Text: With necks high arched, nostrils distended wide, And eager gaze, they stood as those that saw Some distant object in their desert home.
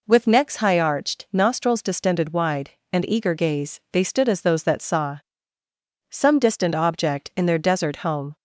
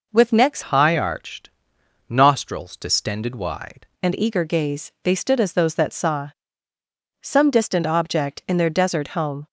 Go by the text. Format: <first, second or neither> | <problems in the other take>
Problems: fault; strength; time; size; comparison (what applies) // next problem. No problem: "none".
first | changes voice from "high" to "wide"; from 0.6 to 3.8 s; 3.2 s long // pauses between "saw" and "Some"; noticeable; at 6.2 s; 0.92 s long; noticeable in the first